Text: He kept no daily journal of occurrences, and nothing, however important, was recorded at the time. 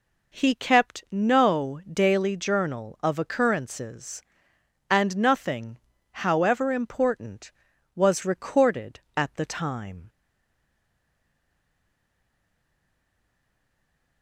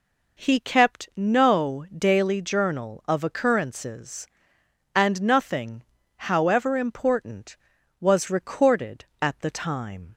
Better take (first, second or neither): second